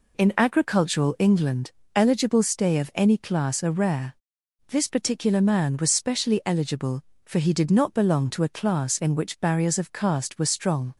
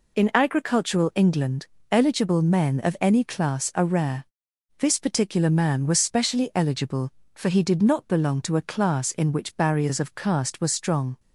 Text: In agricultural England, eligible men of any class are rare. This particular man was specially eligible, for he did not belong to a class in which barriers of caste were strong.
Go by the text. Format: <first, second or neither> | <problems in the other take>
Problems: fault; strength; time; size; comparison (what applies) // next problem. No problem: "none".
second | says "stay" for "men"; at 2.4 s